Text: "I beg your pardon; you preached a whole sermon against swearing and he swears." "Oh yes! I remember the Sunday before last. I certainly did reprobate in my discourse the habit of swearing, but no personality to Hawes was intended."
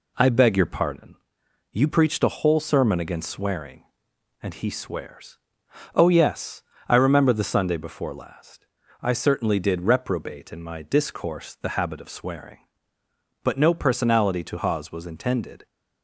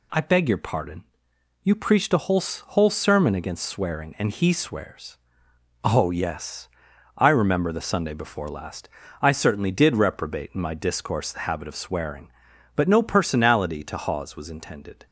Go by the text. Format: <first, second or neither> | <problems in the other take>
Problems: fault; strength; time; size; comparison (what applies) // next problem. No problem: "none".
first | says "whole" twice; at 2.4 s